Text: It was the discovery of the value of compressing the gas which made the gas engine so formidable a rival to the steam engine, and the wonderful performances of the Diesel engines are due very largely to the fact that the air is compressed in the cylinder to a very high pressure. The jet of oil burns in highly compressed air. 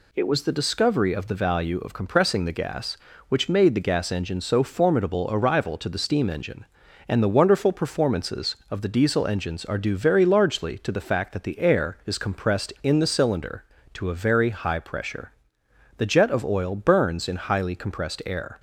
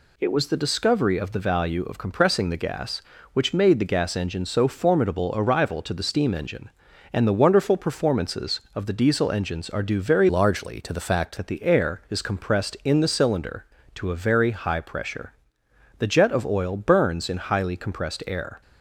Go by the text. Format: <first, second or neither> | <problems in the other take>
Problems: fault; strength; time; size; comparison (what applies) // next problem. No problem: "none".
first | changes voice from "largely" to "fact"; from 10.2 to 11.3 s; 1.1 s long